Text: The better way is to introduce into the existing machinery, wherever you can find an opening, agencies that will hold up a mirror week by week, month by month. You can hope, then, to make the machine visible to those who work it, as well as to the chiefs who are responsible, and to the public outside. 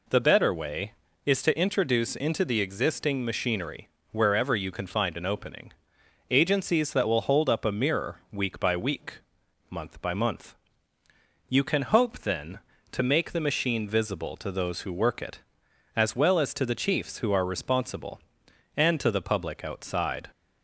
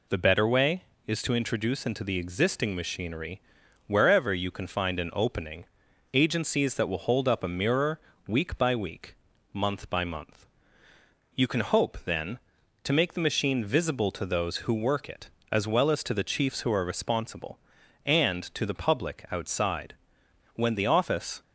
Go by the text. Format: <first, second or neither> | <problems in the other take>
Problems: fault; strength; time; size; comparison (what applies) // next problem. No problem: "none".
first | pauses between "mirror" and "week"; slight; at 7.9 s; 0.26 s long // goes on to say "When the office"; noticeable; from 20.5 s on; 0.88 s long